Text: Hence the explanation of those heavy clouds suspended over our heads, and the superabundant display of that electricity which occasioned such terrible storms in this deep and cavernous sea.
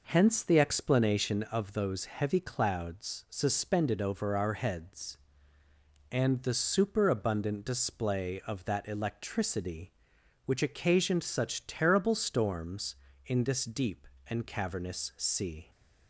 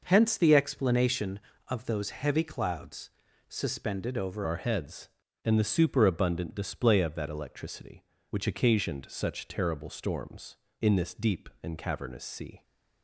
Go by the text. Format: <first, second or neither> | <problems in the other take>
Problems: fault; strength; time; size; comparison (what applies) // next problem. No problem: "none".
first | pauses between "clouds" and "suspended"; at 3.0 s; 0.38 s long // changes voice at "our"; from 4.4 s on; 8.2 s long